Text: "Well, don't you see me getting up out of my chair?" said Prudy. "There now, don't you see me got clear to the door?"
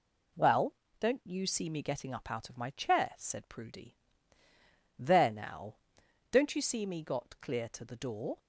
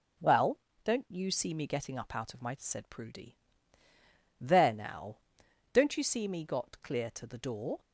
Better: first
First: none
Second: skips "chair"; at 2.5 s

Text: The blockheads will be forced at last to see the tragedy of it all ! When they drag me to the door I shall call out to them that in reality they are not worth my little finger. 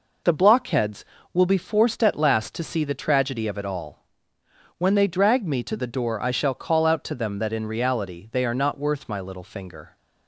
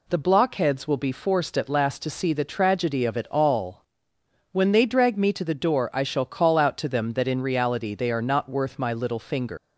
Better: first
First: none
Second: leaves "finger" unfinished; at 9.5 s; 150 ms

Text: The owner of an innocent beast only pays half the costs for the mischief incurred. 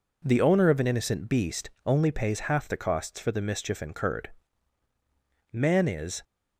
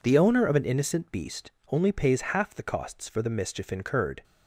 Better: second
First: pauses between "beast" and "only"; slight; at 1.6 s; 0.16 s long // goes on to say "Man is"; noticeable; from 5.5 s on; 0.72 s long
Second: pauses between "beast" and "only"; slight; at 1.5 s; 0.20 s long

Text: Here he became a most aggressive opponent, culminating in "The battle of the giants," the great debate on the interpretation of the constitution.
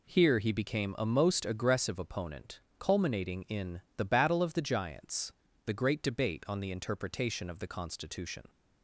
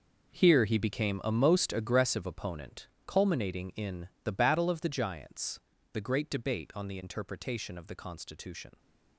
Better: first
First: pauses between "in" and "The"; slight; at 3.8 s; 0.16 s long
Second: gets quieter; strong; throughout; 12.5 dB // pauses between "in" and "The"; slight; at 4.0 s; 0.16 s long

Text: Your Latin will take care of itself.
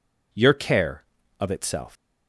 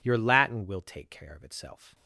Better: second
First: skips "Latin will take"; at 0.5 s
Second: none

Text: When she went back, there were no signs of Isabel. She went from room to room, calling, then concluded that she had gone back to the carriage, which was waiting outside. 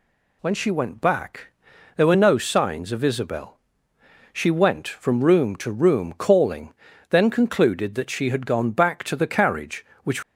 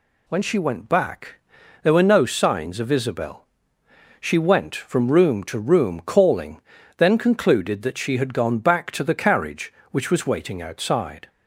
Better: second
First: stops before "was waiting outside"; at 10.2 s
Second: none

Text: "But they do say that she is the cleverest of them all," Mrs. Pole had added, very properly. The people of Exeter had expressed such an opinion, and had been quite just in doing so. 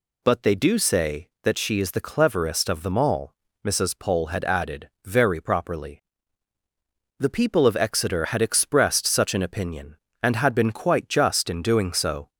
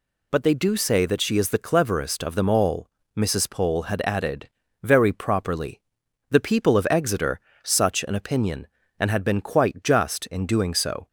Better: first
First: none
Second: skips "had expressed"; at 7.5 s

